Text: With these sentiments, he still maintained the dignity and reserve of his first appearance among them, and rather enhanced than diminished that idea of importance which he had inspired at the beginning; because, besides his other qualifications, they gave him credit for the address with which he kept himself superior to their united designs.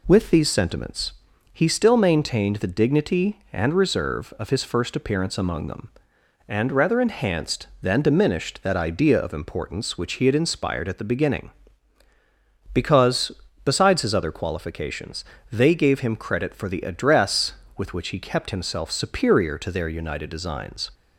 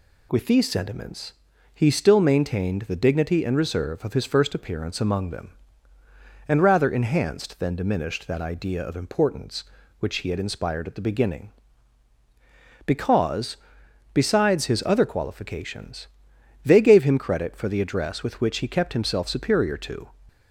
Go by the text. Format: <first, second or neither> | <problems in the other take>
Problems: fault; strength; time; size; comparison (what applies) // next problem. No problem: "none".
first | stops before "their united designs"; at 20.2 s